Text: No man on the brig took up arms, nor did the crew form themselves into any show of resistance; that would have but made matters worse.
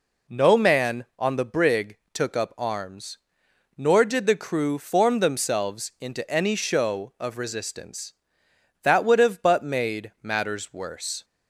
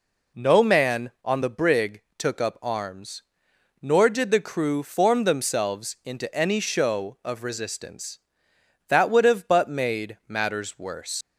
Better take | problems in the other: first | pauses between "brig" and "took"; slight; at 2.0 s; 0.16 s long; slight in the first // leaves "worse" unfinished; at 11.2 s; 90 ms

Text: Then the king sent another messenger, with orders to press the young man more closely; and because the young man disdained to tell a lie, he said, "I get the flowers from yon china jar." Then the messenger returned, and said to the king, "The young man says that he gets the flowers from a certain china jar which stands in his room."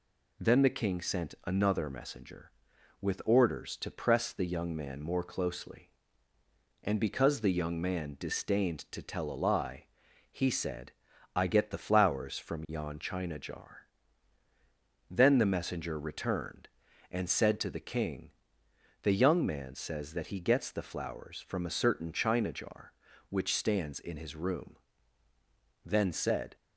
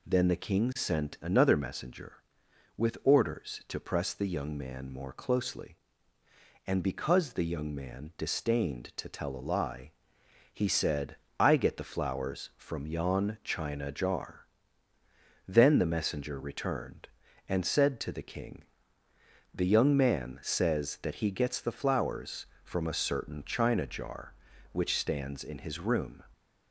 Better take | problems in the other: second | goes on to say "Then said"; noticeable; from 25.8 s on; 0.70 s long

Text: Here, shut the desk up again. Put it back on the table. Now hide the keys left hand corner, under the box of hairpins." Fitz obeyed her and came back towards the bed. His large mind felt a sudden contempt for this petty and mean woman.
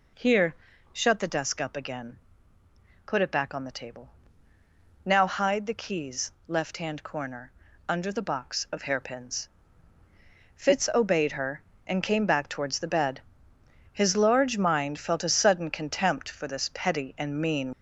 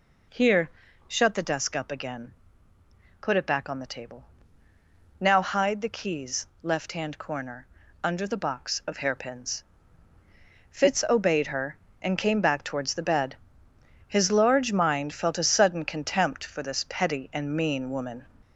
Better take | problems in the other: second | pauses between "keys" and "left"; slight; at 6.3 s; 0.16 s long; slight in the second // stops before "woman"; at 17.7 s

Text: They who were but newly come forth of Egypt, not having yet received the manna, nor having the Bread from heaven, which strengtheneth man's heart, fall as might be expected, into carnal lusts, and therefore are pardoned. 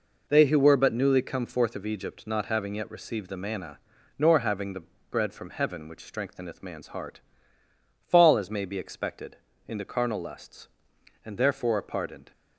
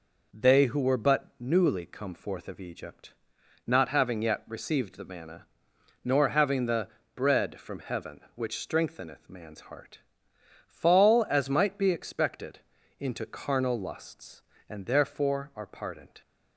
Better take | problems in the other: second | pauses between "the" and "Bread"; slight; at 4.8 s; 0.28 s long; slight in the second // says "may" for "might"; at 8.5 s

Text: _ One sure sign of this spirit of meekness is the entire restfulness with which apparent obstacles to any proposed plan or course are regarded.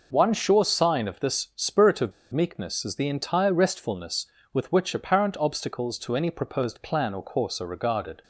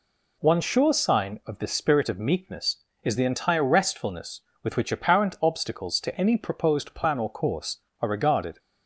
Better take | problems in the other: second | pauses between "of" and "meekness"; slight; at 2.1 s; 0.20 s long

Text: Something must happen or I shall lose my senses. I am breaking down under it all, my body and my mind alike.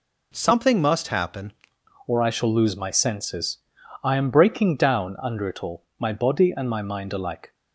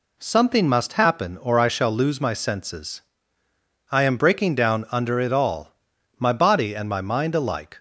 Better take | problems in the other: second | changes voice at "or"; from 2.0 s on; 5.5 s long

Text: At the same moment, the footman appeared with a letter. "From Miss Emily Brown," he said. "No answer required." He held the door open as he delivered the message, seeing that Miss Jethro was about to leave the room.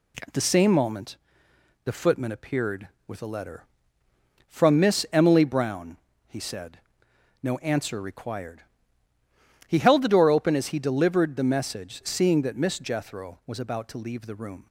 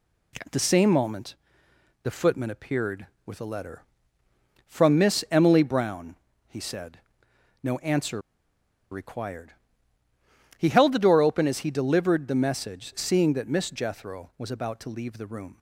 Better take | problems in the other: first | pauses between "answer" and "required"; noticeable; at 8.2 s; 0.71 s long

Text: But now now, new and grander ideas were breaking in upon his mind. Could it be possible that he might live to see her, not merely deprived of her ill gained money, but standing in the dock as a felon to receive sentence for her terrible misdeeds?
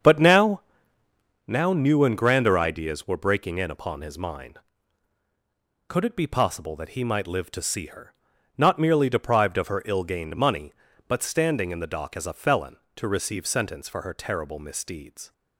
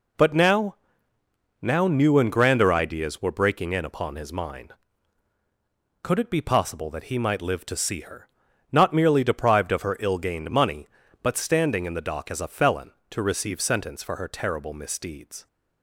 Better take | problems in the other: second | starts louder than the rest; strong; until 1.5 s; 7 dB // pauses between "now" and "now"; noticeable; at 0.6 s; 0.86 s long; noticeable in the second

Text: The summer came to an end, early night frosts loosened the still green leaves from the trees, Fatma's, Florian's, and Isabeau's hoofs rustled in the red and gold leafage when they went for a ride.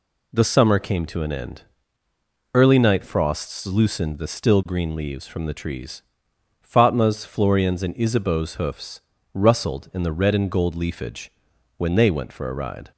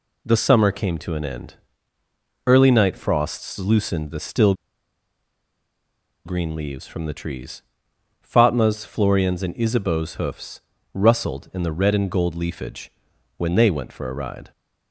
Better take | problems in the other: first | pauses between "still" and "green"; strong; at 4.5 s; 1.7 s long // pauses between "hoofs" and "rustled"; slight; at 10.6 s; 0.32 s long; slight in the first // pauses between "leafage" and "when"; noticeable; at 12.9 s; 0.46 s long; noticeable in the first

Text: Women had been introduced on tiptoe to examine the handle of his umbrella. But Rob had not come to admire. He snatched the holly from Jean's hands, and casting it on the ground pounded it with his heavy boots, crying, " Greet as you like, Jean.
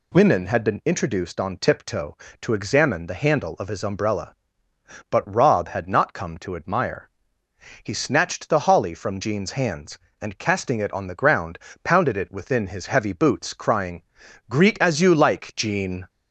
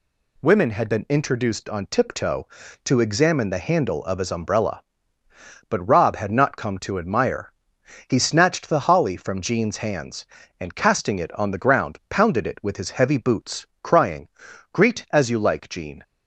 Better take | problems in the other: second | pauses between "ground" and "pounded"; slight; at 11.5 s; 0.28 s long // says "within" for "with"; at 12.2 s

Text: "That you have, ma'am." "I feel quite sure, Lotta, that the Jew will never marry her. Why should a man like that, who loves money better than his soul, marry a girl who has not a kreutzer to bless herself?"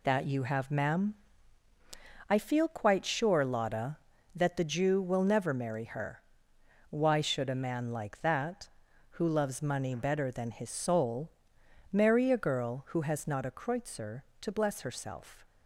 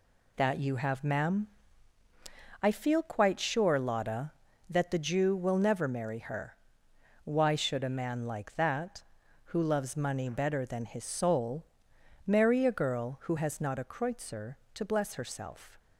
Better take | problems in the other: neither | none

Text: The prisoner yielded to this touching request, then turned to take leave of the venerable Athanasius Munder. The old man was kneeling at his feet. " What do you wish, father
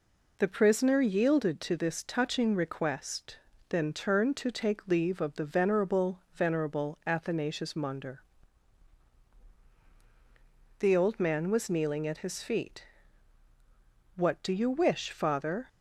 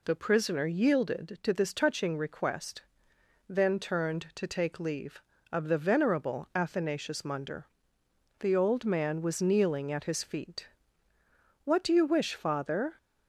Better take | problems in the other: second | says "venerable" twice; at 6.3 s

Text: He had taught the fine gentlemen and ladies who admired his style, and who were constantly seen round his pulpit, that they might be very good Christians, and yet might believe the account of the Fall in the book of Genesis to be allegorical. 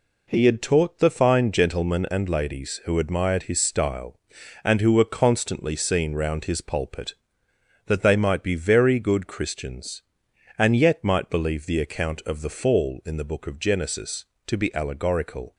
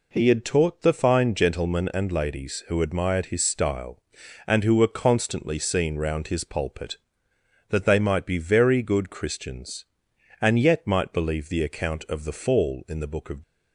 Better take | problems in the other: first | stops before "Genesis to be allegorical"; at 13.4 s

